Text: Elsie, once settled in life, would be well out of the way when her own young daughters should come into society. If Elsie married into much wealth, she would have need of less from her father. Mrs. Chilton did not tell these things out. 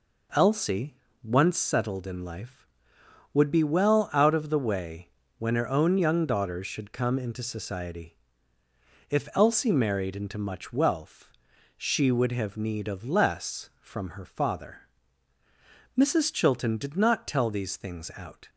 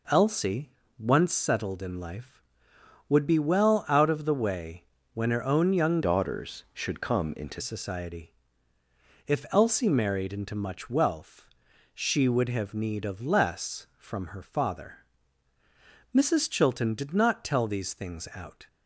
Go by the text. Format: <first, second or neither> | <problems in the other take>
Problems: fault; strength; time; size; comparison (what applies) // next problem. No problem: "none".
first | pauses between "way" and "when"; slight; at 4.8 s; 0.30 s long; slight in the first // changes voice from "daughters" to "into"; from 6.0 to 7.6 s; 1.6 s long